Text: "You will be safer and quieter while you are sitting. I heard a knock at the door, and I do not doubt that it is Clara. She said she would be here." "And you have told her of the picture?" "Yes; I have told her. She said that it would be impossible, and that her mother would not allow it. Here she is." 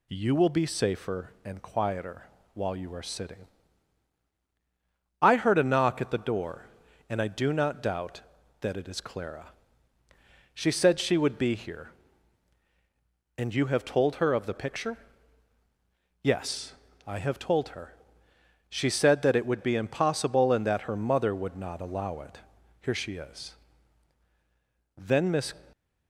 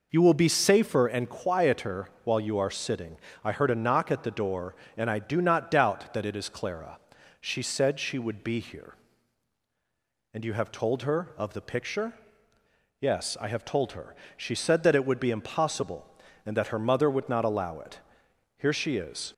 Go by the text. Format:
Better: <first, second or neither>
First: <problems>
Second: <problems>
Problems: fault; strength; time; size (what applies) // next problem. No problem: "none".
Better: second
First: pauses between "quieter" and "while"; slight; at 2.2 s; 0.32 s long // goes on to say "Then Miss"; from 24.9 s on; 0.56 s long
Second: pauses between "quieter" and "while"; slight; at 2.0 s; 0.16 s long